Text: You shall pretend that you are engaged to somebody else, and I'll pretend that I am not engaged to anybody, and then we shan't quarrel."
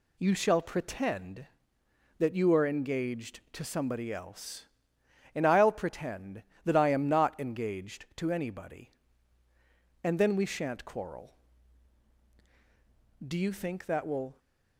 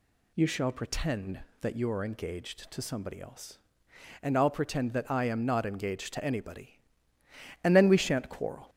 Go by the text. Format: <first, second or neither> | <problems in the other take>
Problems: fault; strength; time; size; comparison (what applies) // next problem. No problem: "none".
second | goes on to say "Do you think that will"; noticeable; from 13.2 s on; 1.1 s long